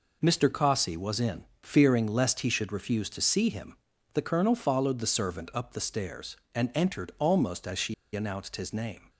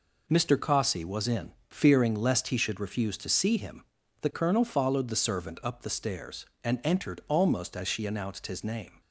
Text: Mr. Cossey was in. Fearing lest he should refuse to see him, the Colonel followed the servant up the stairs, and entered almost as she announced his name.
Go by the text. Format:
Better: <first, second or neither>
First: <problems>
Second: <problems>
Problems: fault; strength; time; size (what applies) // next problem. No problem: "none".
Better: second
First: pauses between "she" and "announced"; slight; at 7.9 s; 0.19 s long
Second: none